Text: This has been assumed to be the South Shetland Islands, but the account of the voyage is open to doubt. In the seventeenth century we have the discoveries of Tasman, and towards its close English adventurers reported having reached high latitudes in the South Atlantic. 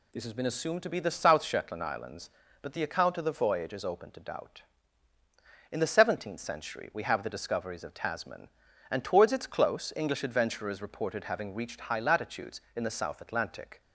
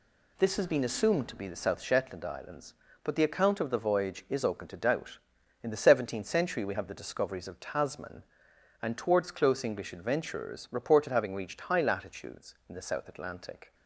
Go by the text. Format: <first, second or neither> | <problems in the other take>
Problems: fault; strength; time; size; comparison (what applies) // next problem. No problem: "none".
first | skips "its"; at 9.2 s